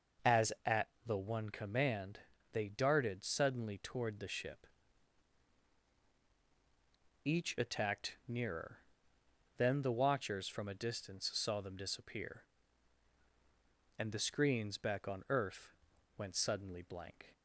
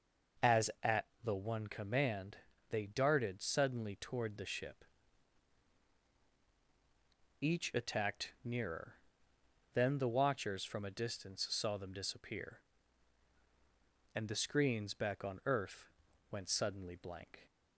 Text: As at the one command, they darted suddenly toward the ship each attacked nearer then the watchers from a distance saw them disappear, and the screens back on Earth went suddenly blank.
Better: neither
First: pauses between "at" and "the"; slight; at 0.8 s; 0.18 s long // pauses between "ship" and "each"; strong; at 4.6 s; 2.5 s long // pauses between "nearer" and "then"; noticeable; at 8.7 s; 0.80 s long // pauses between "Earth" and "went"; at 15.7 s; 0.42 s long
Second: pauses between "at" and "the"; slight; at 1.0 s; 0.18 s long // pauses between "ship" and "each"; strong; at 4.8 s; 2.5 s long // pauses between "nearer" and "then"; noticeable; at 8.9 s; 0.80 s long // pauses between "Earth" and "went"; at 15.9 s; 0.40 s long

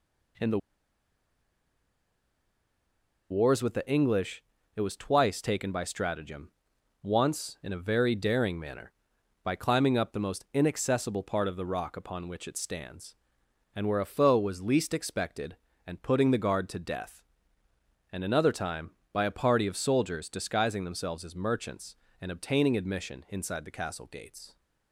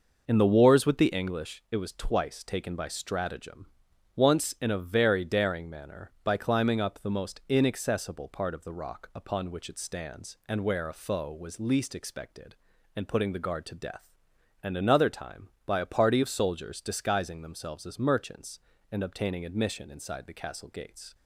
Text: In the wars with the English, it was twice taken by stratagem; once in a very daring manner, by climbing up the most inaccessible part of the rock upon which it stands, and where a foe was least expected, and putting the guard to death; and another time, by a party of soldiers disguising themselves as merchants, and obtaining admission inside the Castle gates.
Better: second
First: pauses between "the" and "wars"; strong; at 0.5 s; 2.7 s long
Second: none

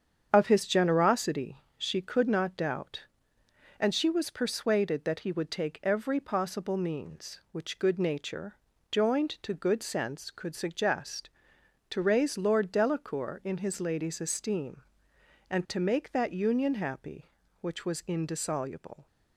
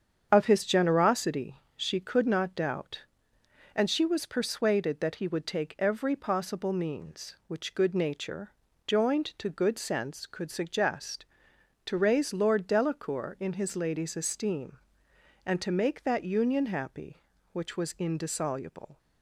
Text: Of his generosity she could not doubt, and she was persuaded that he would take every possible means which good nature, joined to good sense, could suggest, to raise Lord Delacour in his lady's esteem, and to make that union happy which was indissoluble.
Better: neither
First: starts louder than the rest; strong; until 1.3 s; 7.5 dB // pauses between "generosity" and "she"; slight; at 1.6 s; 0.16 s long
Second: starts louder than the rest; strong; until 1.3 s; 7.5 dB // pauses between "generosity" and "she"; slight; at 1.5 s; 0.16 s long

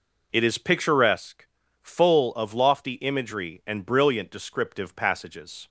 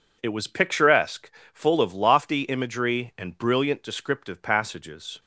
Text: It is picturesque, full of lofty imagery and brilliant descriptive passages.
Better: first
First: none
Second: says "was" for "is"; at 0.3 s

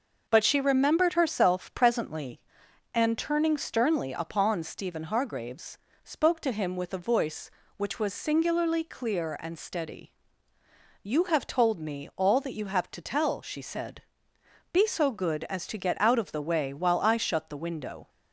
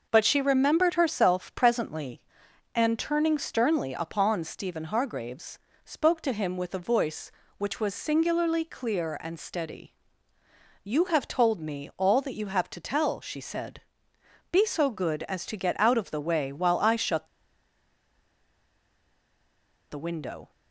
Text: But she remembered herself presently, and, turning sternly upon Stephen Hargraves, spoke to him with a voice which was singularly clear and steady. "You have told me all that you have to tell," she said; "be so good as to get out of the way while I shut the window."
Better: first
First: none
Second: pauses between "shut" and "the"; strong; at 17.2 s; 2.6 s long

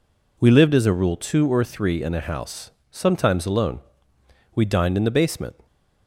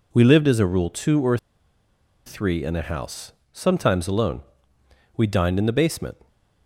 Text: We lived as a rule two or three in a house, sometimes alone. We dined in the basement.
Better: first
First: none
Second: pauses between "or" and "three"; noticeable; at 1.3 s; 0.89 s long

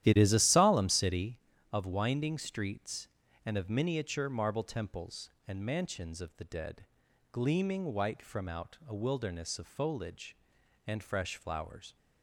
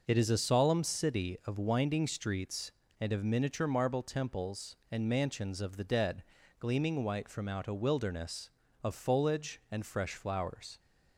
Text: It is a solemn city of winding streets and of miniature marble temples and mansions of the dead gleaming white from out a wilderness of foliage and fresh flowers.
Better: second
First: starts louder than the rest; strong; until 1.4 s; 12 dB // pauses between "dead" and "gleaming"; noticeable; at 6.8 s; 0.46 s long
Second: pauses between "dead" and "gleaming"; at 6.2 s; 0.38 s long

